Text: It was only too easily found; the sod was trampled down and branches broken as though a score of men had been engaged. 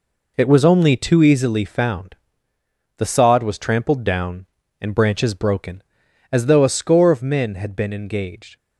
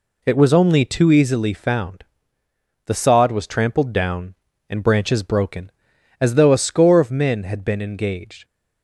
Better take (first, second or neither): second